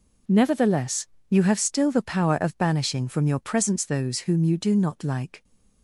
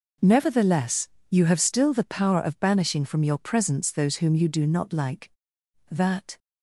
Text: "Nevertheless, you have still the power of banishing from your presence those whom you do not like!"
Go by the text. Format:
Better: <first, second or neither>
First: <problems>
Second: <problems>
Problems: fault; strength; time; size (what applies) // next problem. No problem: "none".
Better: first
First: none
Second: goes on to say "That"; slight; from 5.9 s on; 0.46 s long